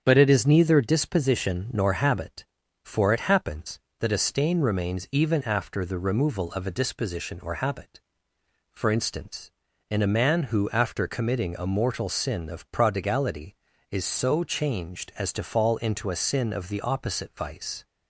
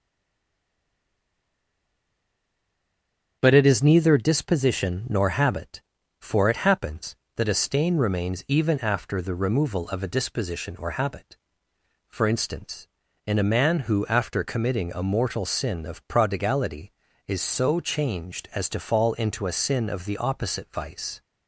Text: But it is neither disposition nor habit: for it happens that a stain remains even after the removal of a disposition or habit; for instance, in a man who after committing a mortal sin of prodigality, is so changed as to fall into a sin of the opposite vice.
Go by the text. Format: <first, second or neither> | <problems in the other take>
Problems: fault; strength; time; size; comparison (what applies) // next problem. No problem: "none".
first | stays silent before the first word; strong; until 3.4 s; 3.4 s long // starts louder than the rest; strong; until 4.4 s; 8 dB; strong in the first